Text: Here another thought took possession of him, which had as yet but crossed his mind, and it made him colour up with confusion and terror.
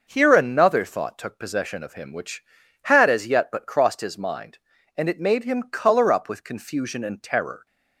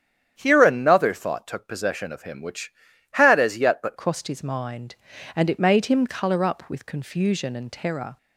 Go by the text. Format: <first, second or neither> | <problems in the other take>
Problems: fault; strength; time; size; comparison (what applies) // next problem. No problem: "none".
first | starts louder than the rest; strong; until 1.3 s; 9 dB; noticeable in the first // changes voice at "crossed"; from 3.9 s on; 4.2 s long